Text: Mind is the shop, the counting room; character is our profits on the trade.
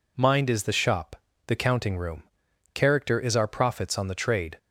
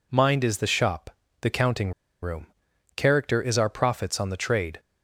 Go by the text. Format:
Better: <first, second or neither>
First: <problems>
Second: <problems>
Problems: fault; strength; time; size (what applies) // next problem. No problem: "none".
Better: first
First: none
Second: pauses between "counting" and "room"; slight; at 1.9 s; 0.31 s long